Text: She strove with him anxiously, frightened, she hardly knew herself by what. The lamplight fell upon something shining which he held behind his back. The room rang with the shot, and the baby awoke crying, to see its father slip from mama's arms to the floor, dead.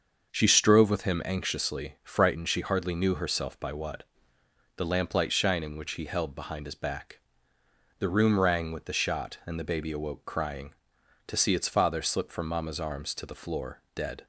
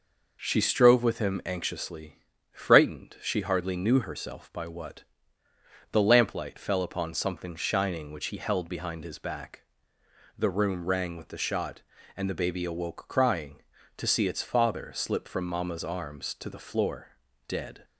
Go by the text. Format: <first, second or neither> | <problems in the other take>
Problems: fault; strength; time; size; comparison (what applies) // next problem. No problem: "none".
second | starts louder than the rest; until 1.3 s; 6.5 dB // skips "fell upon something"; at 5.3 s